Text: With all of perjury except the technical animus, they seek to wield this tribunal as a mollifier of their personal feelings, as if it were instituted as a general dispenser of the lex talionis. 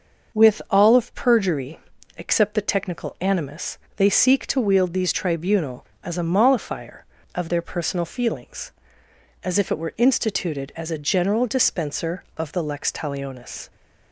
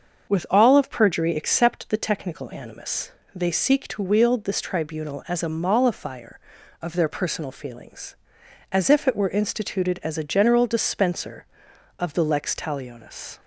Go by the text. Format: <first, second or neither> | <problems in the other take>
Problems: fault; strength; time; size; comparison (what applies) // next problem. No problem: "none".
second | starts louder than the rest; noticeable; until 1.4 s; 6 dB; also in the second // pauses between "perjury" and "except"; at 1.7 s; 0.40 s long // says "these" for "this"; at 4.9 s